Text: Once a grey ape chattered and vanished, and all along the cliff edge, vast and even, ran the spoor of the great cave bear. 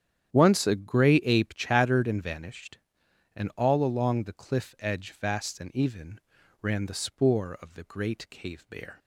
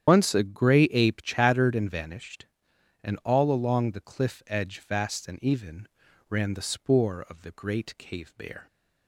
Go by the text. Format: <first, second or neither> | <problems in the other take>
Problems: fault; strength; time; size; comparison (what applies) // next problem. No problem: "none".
first | loses the start of "Once"; at 0.0 s; 75 ms // starts louder than the rest; strong; until 1.0 s; 9.5 dB; strong in the first